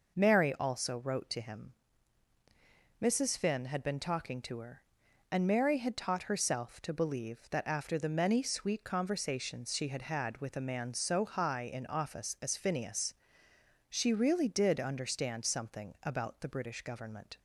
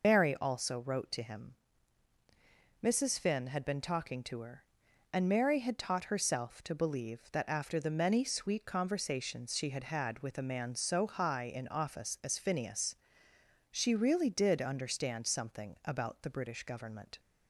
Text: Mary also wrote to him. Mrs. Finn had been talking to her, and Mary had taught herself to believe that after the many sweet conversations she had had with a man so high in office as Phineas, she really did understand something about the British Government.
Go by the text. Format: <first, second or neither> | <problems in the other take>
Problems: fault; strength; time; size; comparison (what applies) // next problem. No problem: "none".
first | loses the start of "Mary"; at 0.0 s; 70 ms